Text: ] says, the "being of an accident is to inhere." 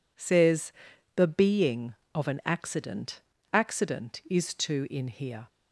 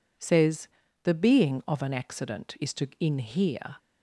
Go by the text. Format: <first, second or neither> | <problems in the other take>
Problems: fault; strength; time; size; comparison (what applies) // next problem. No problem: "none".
second | says "accident" twice; at 3.5 s